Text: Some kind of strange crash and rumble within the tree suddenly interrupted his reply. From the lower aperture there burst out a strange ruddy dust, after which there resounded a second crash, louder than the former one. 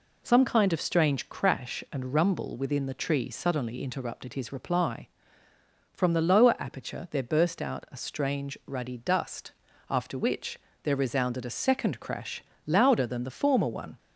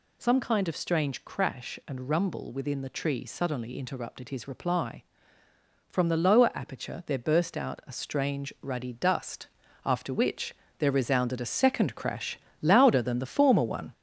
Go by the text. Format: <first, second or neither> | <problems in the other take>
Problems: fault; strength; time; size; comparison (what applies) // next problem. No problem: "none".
first | gets louder; noticeable; throughout; 4.5 dB // pauses between "which" and "there"; slight; at 10.5 s; 0.26 s long; slight in the first